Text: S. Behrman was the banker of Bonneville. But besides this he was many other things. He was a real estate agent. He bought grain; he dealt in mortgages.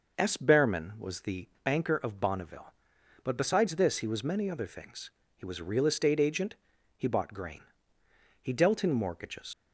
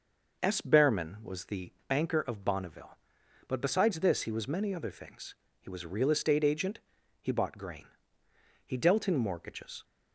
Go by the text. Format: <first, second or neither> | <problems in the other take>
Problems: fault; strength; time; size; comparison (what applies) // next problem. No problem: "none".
second | pauses between "the" and "banker"; slight; at 1.4 s; 0.16 s long; slight in the second // leaves "mortgages" unfinished; at 9.5 s; 55 ms